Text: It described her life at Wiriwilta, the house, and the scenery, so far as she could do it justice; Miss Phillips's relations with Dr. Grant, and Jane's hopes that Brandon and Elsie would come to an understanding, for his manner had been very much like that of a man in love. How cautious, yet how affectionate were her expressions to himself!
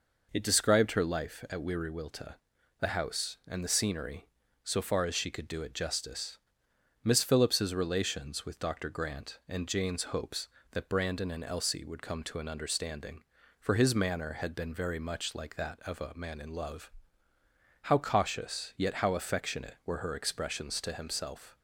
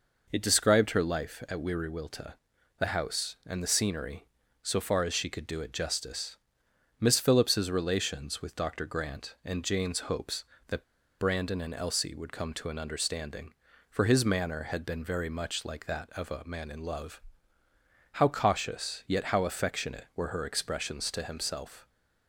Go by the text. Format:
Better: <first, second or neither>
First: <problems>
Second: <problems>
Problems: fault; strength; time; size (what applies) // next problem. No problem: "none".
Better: first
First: none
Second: pauses between "that" and "Brandon"; slight; at 10.8 s; 0.33 s long